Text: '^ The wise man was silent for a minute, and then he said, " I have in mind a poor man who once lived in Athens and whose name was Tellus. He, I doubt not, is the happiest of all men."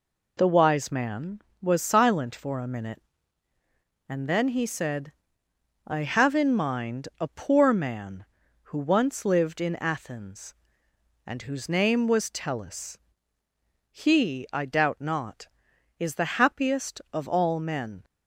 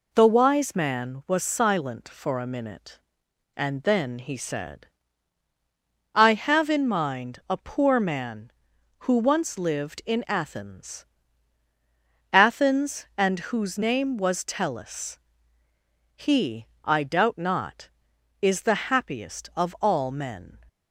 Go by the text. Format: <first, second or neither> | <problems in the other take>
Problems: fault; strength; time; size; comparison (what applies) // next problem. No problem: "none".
first | says "Athens" twice; at 12.3 s